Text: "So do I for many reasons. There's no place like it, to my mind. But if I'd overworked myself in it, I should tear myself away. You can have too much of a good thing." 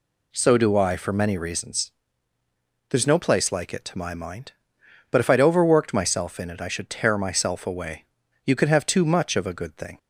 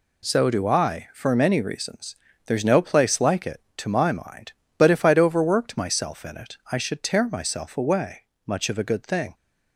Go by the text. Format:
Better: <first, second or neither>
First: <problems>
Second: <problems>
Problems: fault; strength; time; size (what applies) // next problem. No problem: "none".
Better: first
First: none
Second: skips "You can have too"; at 8.3 s